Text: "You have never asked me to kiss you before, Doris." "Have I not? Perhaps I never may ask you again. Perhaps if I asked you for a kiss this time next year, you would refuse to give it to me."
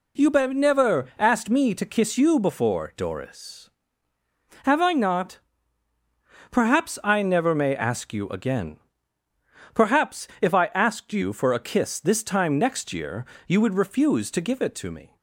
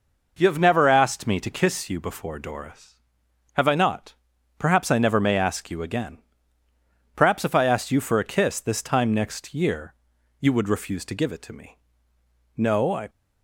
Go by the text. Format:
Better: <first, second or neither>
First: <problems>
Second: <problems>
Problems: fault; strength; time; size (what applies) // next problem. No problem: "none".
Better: first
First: none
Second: goes on to say "No I"; from 12.5 s on; 0.54 s long